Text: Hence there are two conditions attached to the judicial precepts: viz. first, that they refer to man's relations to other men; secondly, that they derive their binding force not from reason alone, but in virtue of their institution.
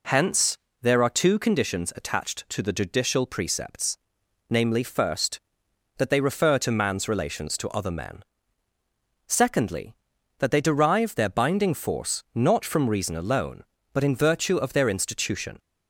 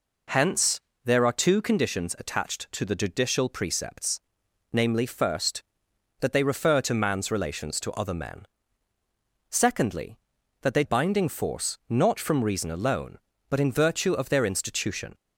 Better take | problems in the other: first | pauses between "Hence" and "there"; slight; at 0.7 s; 0.26 s long; slight in the first // skips "derive their"; at 10.8 s

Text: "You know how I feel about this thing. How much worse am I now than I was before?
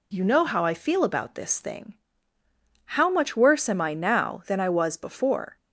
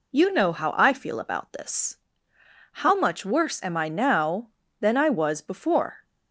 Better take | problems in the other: first | skips "thing"; at 2.3 s

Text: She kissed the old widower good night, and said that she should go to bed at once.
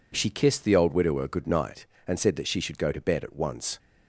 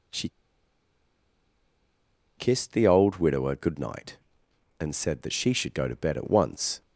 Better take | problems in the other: first | pauses between "She" and "kissed"; strong; at 0.2 s; 2.0 s long

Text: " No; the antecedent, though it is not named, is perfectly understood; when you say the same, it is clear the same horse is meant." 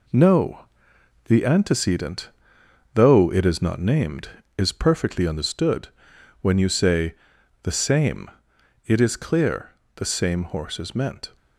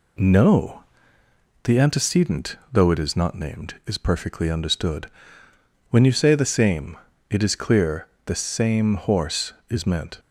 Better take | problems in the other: second | gets quieter; noticeable; throughout; 4 dB // pauses between "say" and "the"; noticeable; at 7.1 s; 0.50 s long // pauses between "clear" and "the"; slight; at 9.7 s; 0.24 s long; slight in the second

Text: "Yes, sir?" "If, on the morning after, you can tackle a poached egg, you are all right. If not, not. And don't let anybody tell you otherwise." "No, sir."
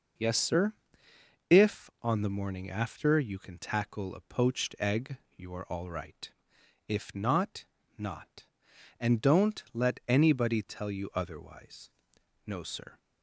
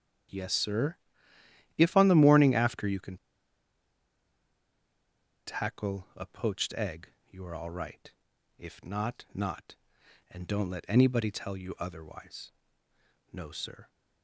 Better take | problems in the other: first | starts louder than the rest; strong; until 2.1 s; 8.5 dB // pauses between "can" and "tackle"; strong; at 3.1 s; 2.3 s long

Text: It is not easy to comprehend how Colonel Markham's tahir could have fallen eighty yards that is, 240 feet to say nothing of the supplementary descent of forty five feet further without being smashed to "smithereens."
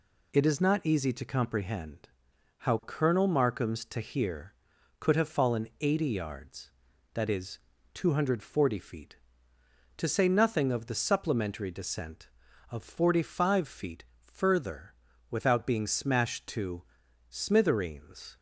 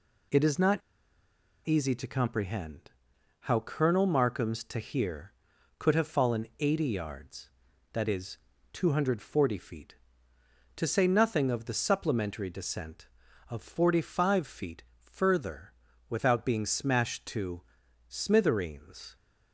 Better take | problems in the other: first | pauses between "not" and "easy"; noticeable; at 0.8 s; 0.86 s long // pauses between "comprehend" and "how"; noticeable; at 2.9 s; 0.50 s long; noticeable in the first // pauses between "feet" and "further"; slight; at 14.8 s; 0.16 s long; slight in the first // pauses between "further" and "without"; at 15.7 s; 0.38 s long; also in the first // pauses between "to" and "smithereens"; noticeable; at 17.6 s; 0.46 s long; noticeable in the first

